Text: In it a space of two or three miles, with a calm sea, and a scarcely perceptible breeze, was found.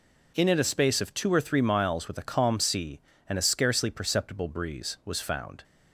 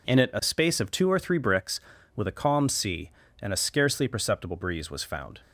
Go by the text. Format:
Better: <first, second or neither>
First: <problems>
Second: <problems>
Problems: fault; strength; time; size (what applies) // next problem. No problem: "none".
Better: first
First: none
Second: says "bricks" for "miles"; at 1.3 s